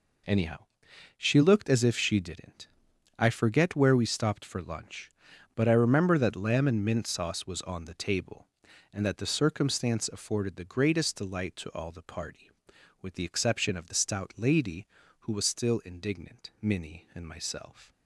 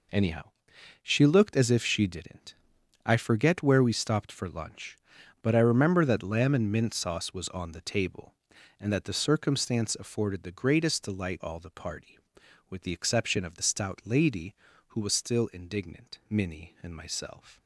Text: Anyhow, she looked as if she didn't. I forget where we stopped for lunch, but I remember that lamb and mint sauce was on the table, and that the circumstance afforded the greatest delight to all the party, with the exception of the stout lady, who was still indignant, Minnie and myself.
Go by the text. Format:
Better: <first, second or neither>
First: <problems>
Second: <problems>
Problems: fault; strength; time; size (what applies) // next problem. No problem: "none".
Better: first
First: none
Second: skips "to"; at 11.4 s